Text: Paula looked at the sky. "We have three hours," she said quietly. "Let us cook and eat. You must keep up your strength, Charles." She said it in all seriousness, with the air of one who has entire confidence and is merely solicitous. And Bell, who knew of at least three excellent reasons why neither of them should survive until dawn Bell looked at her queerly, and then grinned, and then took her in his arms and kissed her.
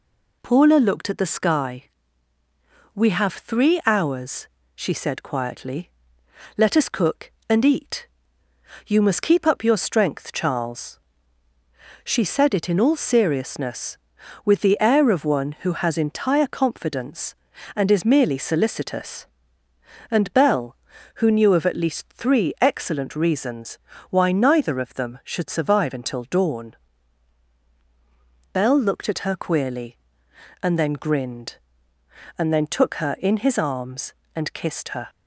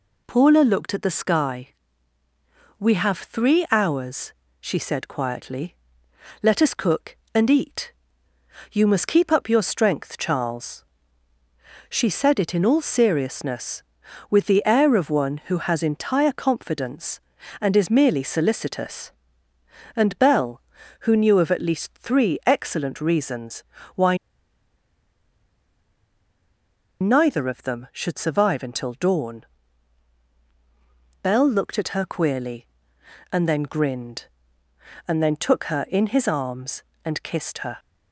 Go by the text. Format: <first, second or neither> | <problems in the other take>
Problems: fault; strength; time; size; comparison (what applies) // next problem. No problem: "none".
first | pauses between "reasons" and "why"; slight; at 23.6 s; 0.32 s long; slight in the first // pauses between "why" and "neither"; strong; at 24.1 s; 2.8 s long // pauses between "dawn" and "Bell"; strong; at 29.4 s; 1.7 s long; strong in the first